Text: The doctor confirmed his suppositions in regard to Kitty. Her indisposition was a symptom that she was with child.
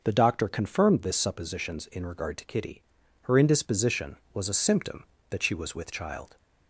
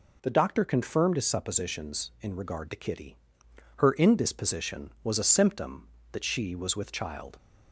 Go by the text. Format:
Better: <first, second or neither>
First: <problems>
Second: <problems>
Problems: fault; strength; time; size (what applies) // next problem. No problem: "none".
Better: second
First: starts louder than the rest; noticeable; until 1.0 s; 6 dB // says "this" for "his"; at 1.0 s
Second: none